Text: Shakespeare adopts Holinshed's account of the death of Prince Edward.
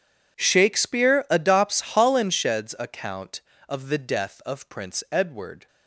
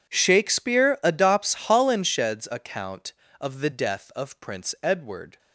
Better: neither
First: none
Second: none

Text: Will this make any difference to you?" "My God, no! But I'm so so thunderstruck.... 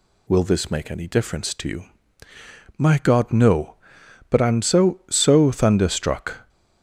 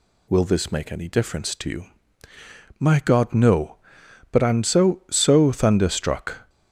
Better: neither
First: none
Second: none

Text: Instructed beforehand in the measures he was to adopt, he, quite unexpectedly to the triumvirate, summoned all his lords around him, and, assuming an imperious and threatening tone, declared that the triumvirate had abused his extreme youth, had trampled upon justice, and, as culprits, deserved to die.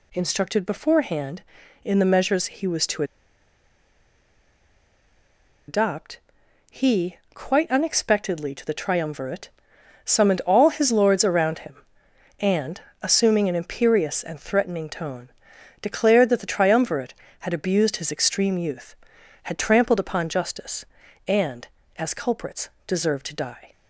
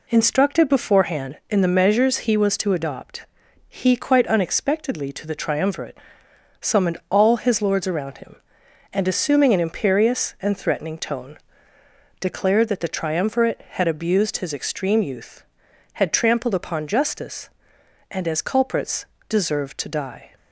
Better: second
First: pauses between "to" and "adopt"; strong; at 3.0 s; 2.6 s long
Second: none

